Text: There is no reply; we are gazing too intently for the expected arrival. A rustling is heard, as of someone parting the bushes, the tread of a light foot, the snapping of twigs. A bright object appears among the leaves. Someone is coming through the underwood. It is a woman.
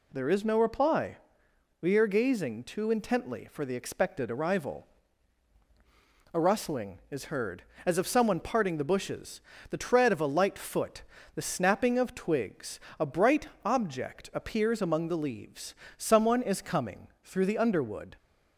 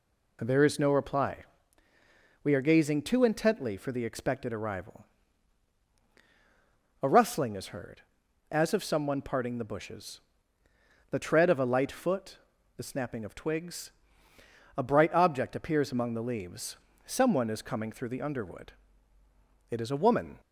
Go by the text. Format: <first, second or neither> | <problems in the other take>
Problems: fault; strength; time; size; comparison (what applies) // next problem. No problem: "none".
second | pauses between "bright" and "object"; slight; at 13.4 s; 0.18 s long // pauses between "coming" and "through"; slight; at 17.0 s; 0.16 s long // stops before "It is a woman"; at 18.1 s